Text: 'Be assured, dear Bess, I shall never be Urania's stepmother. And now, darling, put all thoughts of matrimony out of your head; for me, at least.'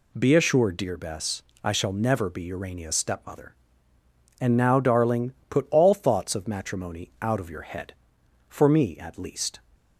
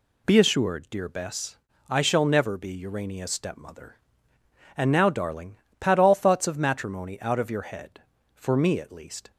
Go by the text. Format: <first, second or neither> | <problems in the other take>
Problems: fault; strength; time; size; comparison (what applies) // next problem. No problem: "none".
first | says "pat" for "put"; at 5.7 s